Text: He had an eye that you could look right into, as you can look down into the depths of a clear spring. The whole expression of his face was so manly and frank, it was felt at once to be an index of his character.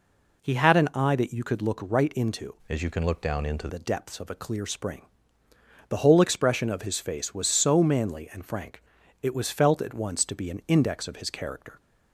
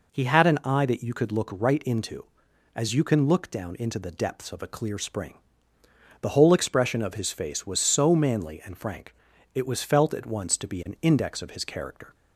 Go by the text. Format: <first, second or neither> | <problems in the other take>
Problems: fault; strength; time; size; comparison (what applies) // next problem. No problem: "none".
second | changes voice from "as" to "into"; from 2.6 to 3.6 s; 1.0 s long